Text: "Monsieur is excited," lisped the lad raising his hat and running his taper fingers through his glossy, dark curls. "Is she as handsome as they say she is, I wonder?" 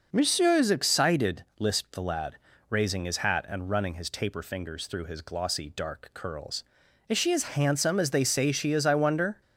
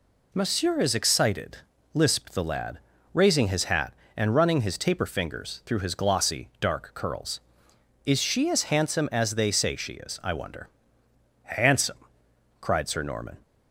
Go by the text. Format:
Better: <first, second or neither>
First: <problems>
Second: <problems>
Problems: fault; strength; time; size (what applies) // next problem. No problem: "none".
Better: first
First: pauses between "lad" and "raising"; slight; at 2.3 s; 0.34 s long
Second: pauses between "lad" and "raising"; slight; at 2.7 s; 0.36 s long // goes on to say "Handsome cried Sir Norman"; strong; from 11.4 s on; 1.9 s long